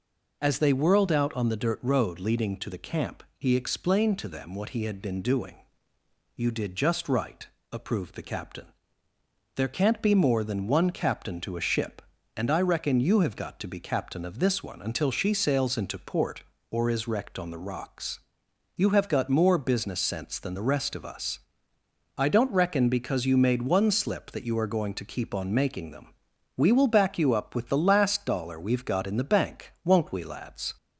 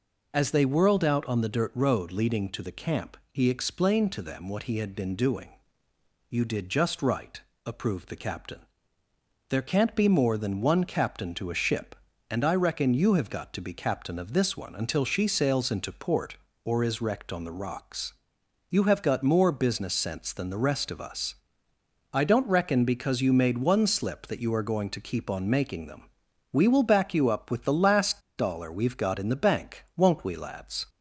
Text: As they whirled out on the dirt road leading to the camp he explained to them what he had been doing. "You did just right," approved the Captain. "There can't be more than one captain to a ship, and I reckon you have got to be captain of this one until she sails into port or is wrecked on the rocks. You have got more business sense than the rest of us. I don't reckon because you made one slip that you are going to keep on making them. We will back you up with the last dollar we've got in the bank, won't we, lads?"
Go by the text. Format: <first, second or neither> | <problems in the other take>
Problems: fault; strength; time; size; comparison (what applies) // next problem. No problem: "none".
first | pauses between "last" and "dollar"; slight; at 28.1 s; 0.18 s long